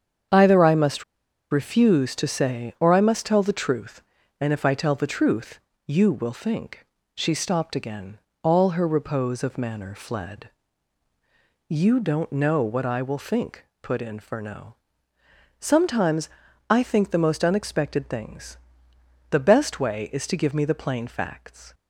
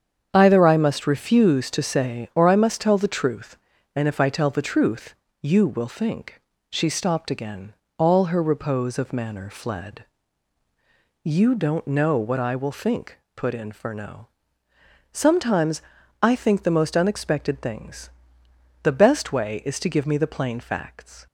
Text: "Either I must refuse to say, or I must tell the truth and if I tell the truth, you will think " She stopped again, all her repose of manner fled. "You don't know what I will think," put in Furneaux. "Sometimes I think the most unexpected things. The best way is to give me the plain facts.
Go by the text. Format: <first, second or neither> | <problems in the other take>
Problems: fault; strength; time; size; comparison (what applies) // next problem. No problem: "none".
second | starts louder than the rest; strong; until 1.7 s; 7.5 dB; strong in the second // pauses between "must" and "refuse"; noticeable; at 1.0 s; 0.47 s long // pauses between "Sometimes" and "I"; at 16.2 s; 0.40 s long; also in the second